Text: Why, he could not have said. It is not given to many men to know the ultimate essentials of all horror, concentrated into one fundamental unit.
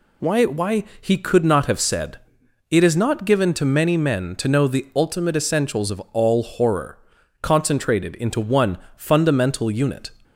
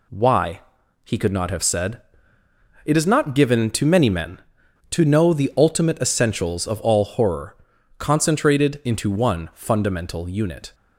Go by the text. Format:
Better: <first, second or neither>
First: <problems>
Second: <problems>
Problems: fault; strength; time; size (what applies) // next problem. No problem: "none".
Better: second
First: says "Why" twice; at 0.4 s // pauses between "one" and "fundamental"; slight; at 8.7 s; 0.20 s long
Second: none